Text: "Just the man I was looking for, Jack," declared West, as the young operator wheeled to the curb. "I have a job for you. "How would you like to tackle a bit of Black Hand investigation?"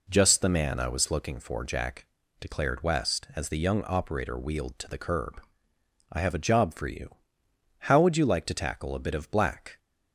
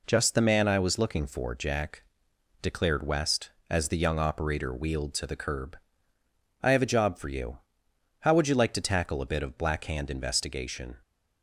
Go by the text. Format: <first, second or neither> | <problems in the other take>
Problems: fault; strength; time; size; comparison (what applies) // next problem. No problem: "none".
second | stops before "Hand investigation"; at 9.7 s